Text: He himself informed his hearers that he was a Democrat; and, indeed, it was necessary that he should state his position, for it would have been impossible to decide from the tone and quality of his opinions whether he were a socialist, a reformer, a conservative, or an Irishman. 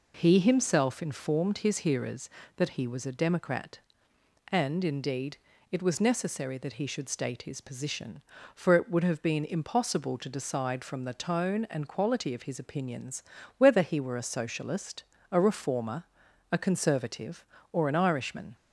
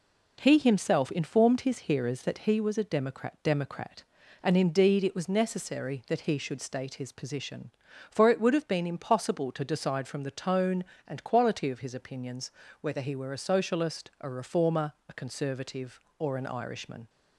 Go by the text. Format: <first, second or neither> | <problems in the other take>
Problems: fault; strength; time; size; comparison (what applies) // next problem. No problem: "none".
first | says "Democrat" twice; at 3.4 s // pauses between "opinions" and "whether"; slight; at 12.5 s; 0.28 s long; slight in the first